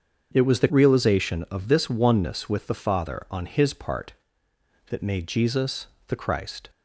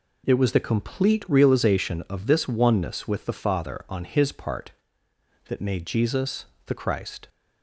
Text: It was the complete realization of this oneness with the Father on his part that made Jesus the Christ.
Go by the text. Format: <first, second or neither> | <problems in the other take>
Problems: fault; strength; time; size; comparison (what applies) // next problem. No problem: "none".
second | starts louder than the rest; until 1.3 s; 7 dB // skips "complete"; at 0.6 s // pauses between "Jesus" and "the"; slight; at 5.8 s; 0.20 s long; slight in the second